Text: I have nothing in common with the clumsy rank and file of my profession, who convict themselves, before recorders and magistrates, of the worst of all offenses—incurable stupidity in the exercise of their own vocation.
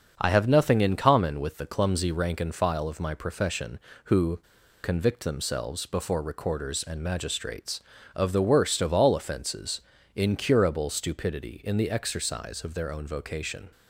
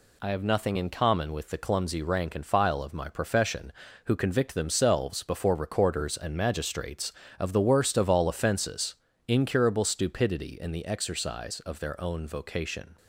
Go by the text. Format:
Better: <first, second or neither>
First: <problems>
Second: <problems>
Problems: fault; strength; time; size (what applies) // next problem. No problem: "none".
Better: second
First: starts louder than the rest; until 1.1 s; 6.5 dB // pauses between "who" and "convict"; at 4.3 s; 0.43 s long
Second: none